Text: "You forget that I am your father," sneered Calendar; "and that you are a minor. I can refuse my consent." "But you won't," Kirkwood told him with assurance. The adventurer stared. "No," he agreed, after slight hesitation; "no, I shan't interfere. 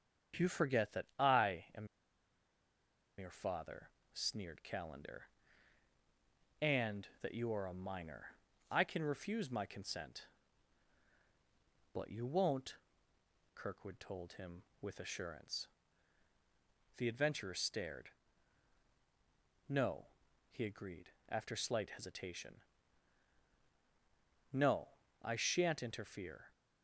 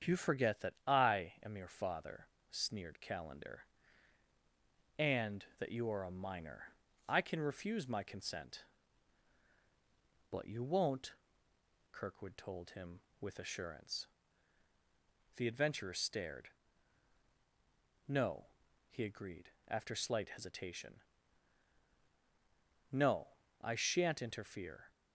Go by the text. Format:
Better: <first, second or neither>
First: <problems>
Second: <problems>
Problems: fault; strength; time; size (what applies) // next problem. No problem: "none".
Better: second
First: starts louder than the rest; strong; until 1.4 s; 8 dB // pauses between "am" and "your"; strong; at 1.8 s; 1.3 s long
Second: starts louder than the rest; strong; until 1.1 s; 8 dB